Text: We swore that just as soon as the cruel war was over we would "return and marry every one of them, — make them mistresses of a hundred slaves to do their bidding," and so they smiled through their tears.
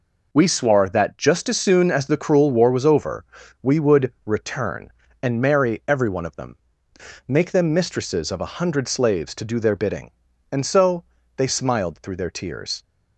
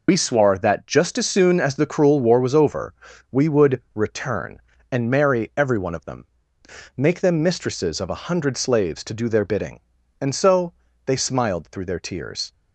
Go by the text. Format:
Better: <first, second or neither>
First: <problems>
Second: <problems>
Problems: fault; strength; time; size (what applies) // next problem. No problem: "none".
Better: first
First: pauses between "over" and "we"; at 3.2 s; 0.40 s long // pauses between "so" and "they"; slight; at 11.0 s; 0.32 s long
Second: loses the start of "We"; at 0.0 s; 65 ms // pauses between "over" and "we"; at 2.9 s; 0.40 s long // pauses between "so" and "they"; slight; at 10.7 s; 0.32 s long